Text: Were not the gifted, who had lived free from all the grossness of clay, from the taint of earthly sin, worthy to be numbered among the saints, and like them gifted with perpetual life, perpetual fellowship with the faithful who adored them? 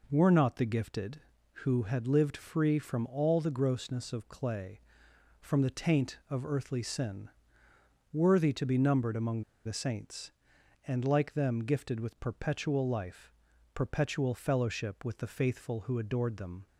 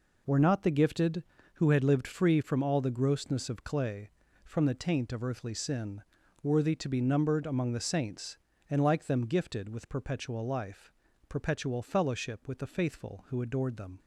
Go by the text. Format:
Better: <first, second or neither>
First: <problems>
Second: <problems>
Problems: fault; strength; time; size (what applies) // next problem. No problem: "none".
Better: second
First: pauses between "among" and "the"; slight; at 9.4 s; 0.24 s long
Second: none